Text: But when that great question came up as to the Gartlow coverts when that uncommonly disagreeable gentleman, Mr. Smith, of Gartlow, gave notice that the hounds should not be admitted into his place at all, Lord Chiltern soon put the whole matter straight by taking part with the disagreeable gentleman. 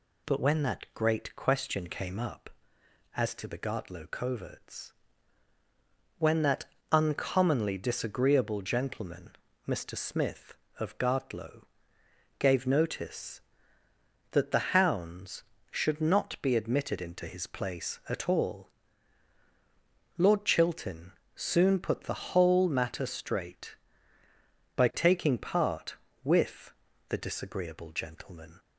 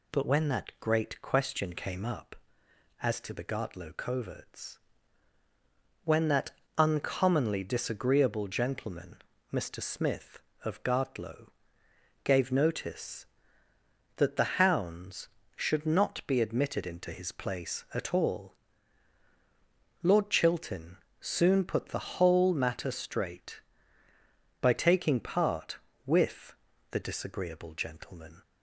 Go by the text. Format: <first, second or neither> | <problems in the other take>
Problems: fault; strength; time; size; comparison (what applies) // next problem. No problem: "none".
neither | pauses between "coverts" and "when"; strong; the same in both // pauses between "that" and "uncommonly"; slight; the same in both // pauses between "Chiltern" and "soon"; slight; the same in both // pauses between "with" and "the"; slight; the same in both